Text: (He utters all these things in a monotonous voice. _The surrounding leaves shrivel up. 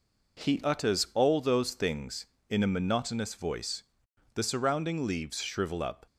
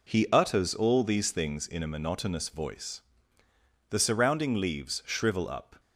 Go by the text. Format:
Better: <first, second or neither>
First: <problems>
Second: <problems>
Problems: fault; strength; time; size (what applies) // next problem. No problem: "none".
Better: second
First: says "those" for "these"; at 1.3 s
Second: none